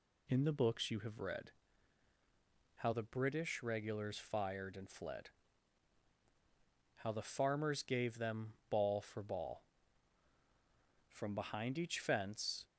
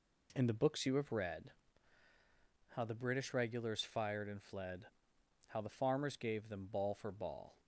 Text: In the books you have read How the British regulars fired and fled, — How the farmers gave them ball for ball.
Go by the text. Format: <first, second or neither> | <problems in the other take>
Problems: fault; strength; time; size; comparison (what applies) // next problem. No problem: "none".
second | pauses between "read" and "How"; strong; at 1.5 s; 1.2 s long; also in the second // goes on to say "From behind each fence"; from 11.1 s on; 1.5 s long